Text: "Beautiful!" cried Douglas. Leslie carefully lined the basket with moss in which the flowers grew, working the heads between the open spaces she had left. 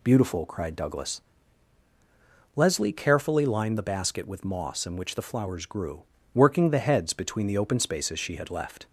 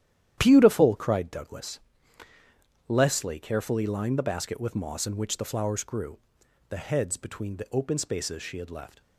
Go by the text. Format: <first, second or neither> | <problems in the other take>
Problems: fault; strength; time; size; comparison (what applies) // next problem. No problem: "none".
first | starts louder than the rest; strong; until 1.3 s; 11 dB // skips "working"; at 6.4 s